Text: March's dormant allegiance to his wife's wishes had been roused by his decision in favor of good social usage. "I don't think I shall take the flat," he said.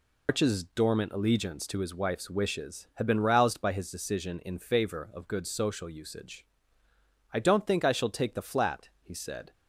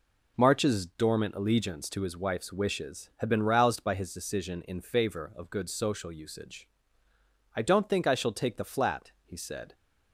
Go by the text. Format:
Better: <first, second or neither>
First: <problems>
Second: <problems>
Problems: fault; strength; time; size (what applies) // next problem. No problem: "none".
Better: second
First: loses the start of "March's"; at 0.2 s; 155 ms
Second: none